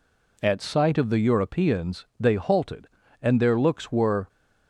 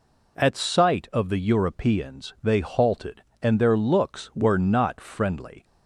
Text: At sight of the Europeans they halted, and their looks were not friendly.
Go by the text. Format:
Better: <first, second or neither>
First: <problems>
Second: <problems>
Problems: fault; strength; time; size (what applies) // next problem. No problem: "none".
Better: second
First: stops before "not friendly"; at 4.2 s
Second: none